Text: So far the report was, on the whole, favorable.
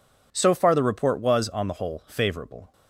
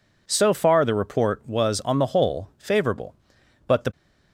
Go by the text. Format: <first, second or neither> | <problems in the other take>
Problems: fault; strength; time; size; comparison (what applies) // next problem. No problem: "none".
first | goes on to say "But the"; slight; from 3.6 s on; 0.24 s long